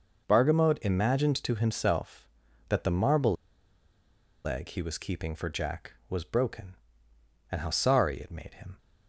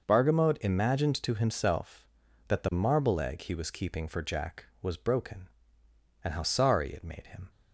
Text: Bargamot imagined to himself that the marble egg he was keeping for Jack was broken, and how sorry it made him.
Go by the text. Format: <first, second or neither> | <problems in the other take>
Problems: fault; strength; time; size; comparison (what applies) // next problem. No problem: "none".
second | pauses between "marble" and "egg"; at 3.3 s; 1.1 s long